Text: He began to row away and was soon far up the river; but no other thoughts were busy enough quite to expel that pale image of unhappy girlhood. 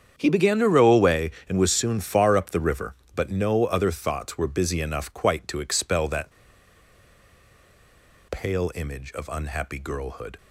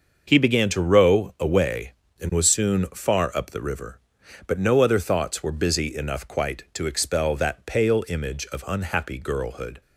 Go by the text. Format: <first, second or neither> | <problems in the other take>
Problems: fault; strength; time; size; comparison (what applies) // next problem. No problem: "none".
second | starts louder than the rest; strong; until 1.2 s; 8.5 dB; also in the second // pauses between "that" and "pale"; strong; at 6.3 s; 1.9 s long